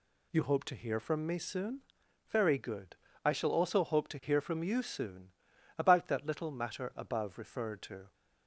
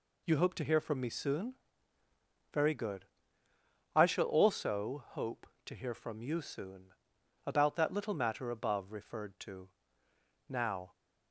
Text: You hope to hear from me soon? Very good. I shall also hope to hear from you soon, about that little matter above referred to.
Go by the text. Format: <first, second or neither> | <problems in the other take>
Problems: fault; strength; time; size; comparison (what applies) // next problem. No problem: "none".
first | goes on to say "Now"; slight; from 10.4 s on; 0.44 s long